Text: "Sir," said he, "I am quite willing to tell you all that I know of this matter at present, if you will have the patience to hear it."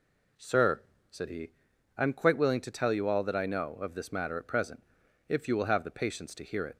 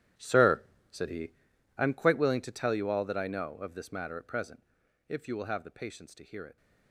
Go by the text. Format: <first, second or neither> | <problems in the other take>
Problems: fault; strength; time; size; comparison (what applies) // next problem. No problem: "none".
first | gets quieter; strong; throughout; 16.5 dB